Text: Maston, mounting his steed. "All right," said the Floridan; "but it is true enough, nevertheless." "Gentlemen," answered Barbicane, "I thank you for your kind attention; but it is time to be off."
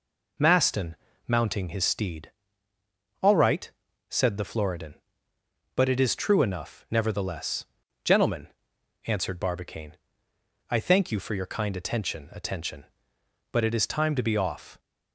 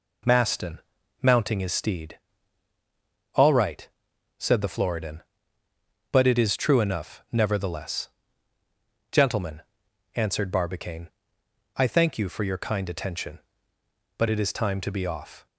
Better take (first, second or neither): second